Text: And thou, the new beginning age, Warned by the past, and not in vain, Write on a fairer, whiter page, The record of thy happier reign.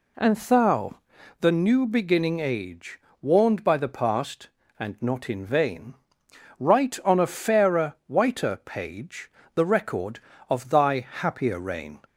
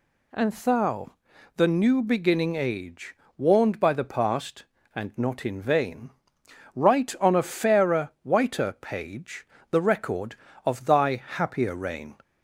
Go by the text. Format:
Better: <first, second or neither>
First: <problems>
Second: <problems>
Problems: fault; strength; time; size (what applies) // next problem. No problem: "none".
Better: second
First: starts louder than the rest; slight; until 1.5 s; 2.5 dB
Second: none